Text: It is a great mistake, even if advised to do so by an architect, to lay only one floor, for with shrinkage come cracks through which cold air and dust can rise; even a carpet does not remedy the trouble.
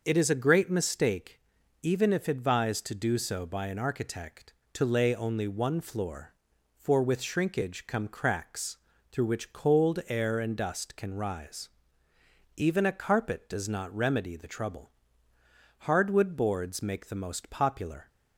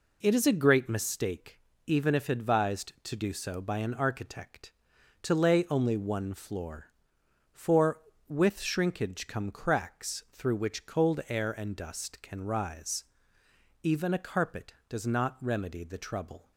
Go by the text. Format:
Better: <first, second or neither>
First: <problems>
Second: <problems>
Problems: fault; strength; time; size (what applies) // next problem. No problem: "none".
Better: second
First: starts louder than the rest; until 1.0 s; 6 dB // pauses between "cracks" and "through"; slight; at 8.7 s; 0.34 s long // goes on to say "Hardwood boards make the most popular"; strong; from 15.8 s on; 2.2 s long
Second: none